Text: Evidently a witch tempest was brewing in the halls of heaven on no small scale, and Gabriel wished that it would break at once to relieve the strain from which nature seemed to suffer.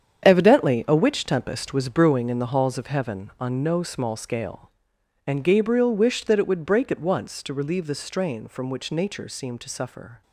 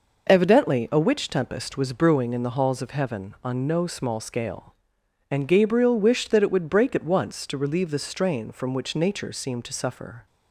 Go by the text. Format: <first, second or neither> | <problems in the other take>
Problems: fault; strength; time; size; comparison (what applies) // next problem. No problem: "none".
second | gets quieter; strong; throughout; 10.5 dB